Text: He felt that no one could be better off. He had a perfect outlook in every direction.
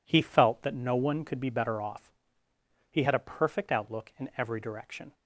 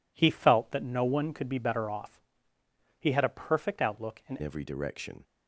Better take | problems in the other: first | changes voice at "every"; from 4.4 s on; 0.8 s long

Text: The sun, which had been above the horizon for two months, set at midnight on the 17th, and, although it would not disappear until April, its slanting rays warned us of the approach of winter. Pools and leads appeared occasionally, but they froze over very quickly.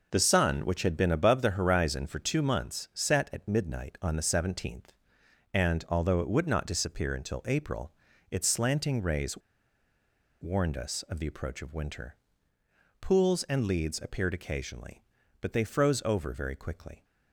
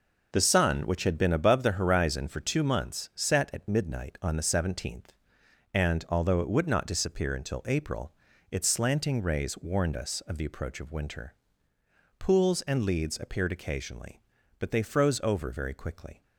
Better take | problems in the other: second | pauses between "rays" and "warned"; at 9.3 s; 1.0 s long

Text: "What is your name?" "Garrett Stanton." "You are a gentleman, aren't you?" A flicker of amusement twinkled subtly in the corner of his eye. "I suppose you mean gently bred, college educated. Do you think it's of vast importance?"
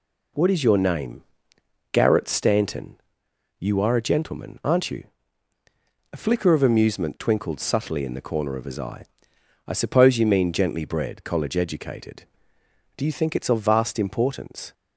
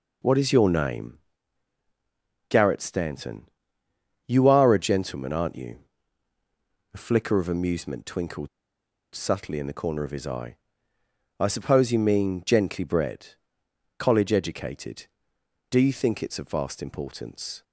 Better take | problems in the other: first | pauses between "twinkled" and "subtly"; noticeable; at 8.4 s; 0.64 s long

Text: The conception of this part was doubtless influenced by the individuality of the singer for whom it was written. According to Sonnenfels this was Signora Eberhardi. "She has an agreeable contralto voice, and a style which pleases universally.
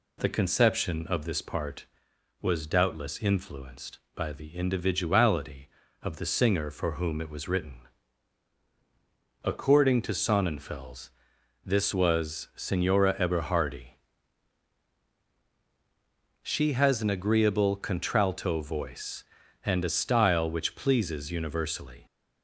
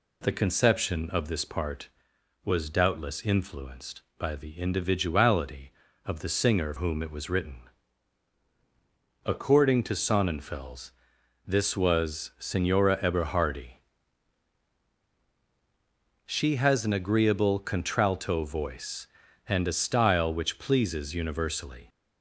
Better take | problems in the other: first | skips "for"; at 6.7 s // pauses between "Sonnenfels" and "this"; noticeable; at 10.9 s; 0.56 s long; noticeable in the first

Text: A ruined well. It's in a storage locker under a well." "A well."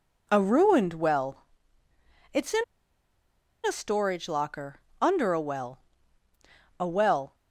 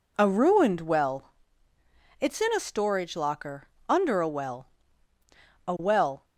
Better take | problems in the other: second | pauses between "in" and "a"; at 2.6 s; 1.0 s long // pauses between "locker" and "under"; slight; at 4.7 s; 0.22 s long; slight in the second

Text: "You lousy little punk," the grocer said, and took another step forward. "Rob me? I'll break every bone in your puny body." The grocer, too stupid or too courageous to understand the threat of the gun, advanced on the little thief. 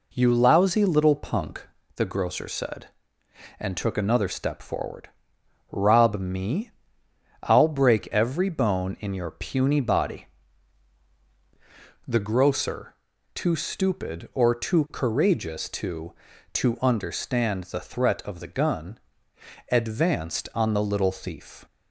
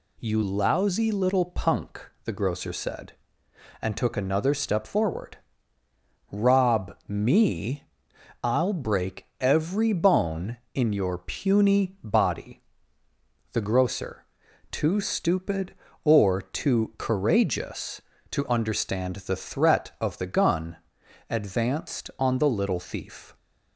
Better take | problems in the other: second | says "to" twice; at 16.5 s

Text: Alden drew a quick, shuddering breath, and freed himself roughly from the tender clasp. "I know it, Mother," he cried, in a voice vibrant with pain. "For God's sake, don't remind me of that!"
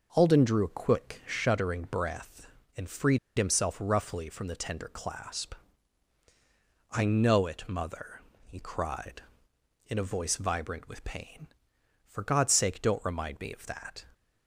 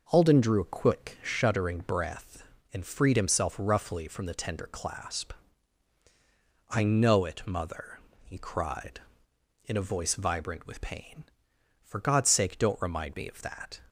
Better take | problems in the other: second | pauses between "freed" and "himself"; slight; at 3.1 s; 0.20 s long

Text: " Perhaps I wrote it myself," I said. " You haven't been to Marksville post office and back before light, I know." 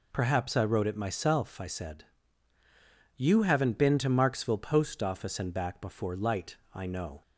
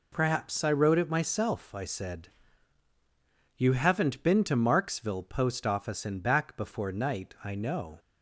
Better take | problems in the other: first | says "night" for "light"; at 6.9 s

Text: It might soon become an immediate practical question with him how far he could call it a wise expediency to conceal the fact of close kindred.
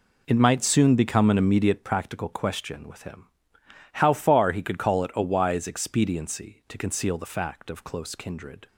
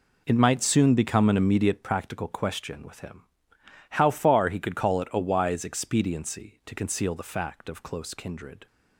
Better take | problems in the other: neither | pauses between "him" and "how"; noticeable; the same in both

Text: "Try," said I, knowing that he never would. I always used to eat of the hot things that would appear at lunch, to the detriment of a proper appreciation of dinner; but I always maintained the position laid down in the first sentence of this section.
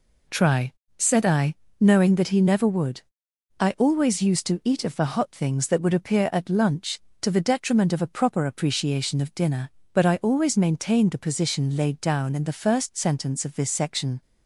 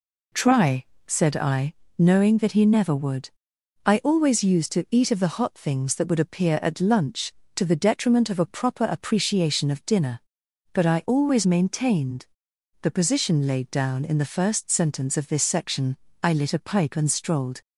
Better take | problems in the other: first | pauses between "maintained" and "the"; noticeable; at 12.2 s; 0.56 s long // goes on to say "I lit a pipe and strolled"; from 16.2 s on; 1.3 s long

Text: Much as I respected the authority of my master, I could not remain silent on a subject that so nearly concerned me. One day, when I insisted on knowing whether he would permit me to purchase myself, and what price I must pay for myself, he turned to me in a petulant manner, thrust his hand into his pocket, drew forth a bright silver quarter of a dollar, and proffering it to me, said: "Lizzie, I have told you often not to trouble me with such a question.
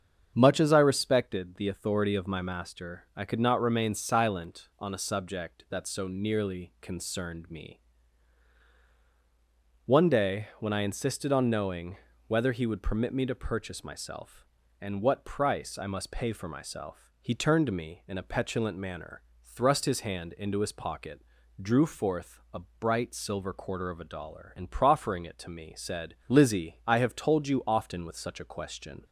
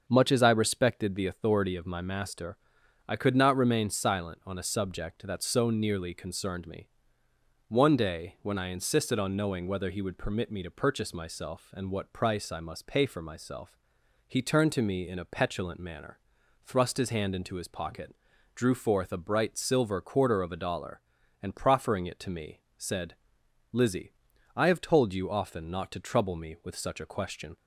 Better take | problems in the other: second | starts louder than the rest; strong; until 1.3 s; 7 dB; also in the second // pauses between "knowing" and "whether"; slight; at 11.9 s; 0.32 s long // pauses between "a" and "bright"; slight; at 22.6 s; 0.18 s long // skips "not to trouble me"; at 28.0 s

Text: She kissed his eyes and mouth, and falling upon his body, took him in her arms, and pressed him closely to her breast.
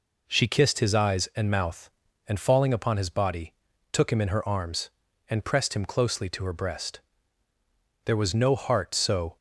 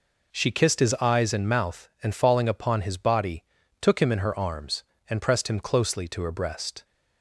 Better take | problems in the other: second | goes on to say "There was no heart so"; from 8.0 s on; 1.3 s long

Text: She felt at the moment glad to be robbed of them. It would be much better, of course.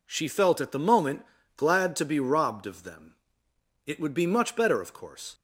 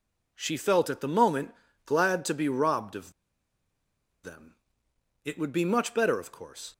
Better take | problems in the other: first | pauses between "moment" and "glad"; slight; at 1.5 s; 0.32 s long; slight in the first // pauses between "of" and "them"; at 3.1 s; 1.1 s long

